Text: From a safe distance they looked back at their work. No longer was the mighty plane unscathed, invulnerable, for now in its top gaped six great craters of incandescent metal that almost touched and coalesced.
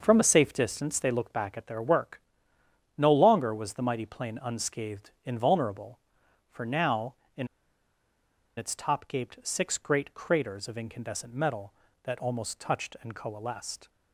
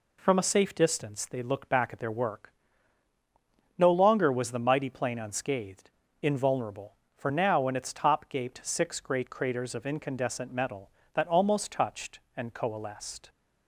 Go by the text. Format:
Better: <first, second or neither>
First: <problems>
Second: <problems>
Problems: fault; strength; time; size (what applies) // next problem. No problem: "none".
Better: second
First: starts louder than the rest; noticeable; until 1.0 s; 6 dB // pauses between "in" and "its"; at 7.4 s; 1.0 s long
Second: none